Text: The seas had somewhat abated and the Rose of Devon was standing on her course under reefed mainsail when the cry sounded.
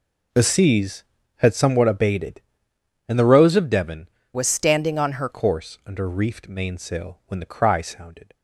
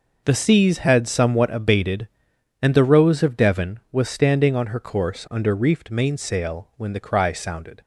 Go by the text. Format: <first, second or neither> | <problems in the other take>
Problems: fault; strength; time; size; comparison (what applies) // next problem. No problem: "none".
second | changes voice from "was" to "her"; from 4.3 to 5.2 s; 0.9 s long